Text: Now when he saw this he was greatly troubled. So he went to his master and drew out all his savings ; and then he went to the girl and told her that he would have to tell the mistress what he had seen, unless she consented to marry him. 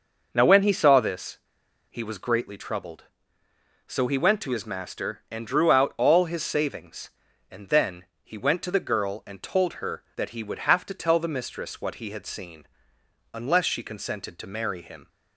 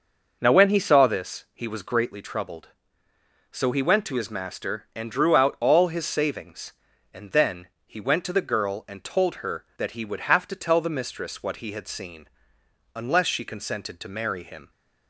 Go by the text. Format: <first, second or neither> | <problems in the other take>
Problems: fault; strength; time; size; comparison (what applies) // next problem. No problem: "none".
second | pauses between "this" and "he"; noticeable; at 1.3 s; 0.52 s long // pauses between "then" and "he"; slight; at 8.0 s; 0.20 s long; slight in the second